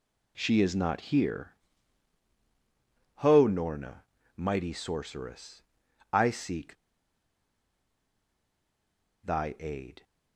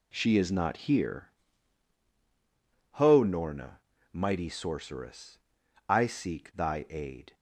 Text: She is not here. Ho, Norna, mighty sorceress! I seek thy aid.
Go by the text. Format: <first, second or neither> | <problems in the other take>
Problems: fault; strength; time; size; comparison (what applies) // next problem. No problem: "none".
second | pauses between "seek" and "thy"; strong; at 6.7 s; 2.4 s long